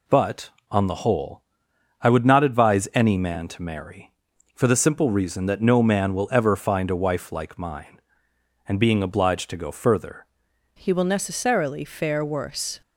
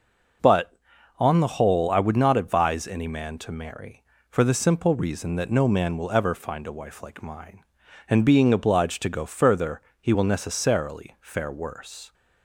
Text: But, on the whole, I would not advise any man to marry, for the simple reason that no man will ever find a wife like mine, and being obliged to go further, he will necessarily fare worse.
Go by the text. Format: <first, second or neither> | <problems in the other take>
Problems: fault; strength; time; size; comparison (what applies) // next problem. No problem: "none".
second | changes voice at "he"; from 10.7 s on; 2.1 s long